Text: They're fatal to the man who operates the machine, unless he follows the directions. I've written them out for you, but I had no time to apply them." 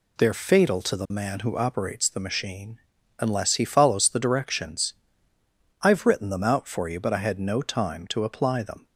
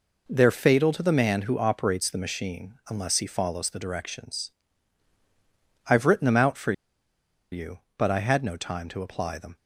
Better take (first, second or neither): first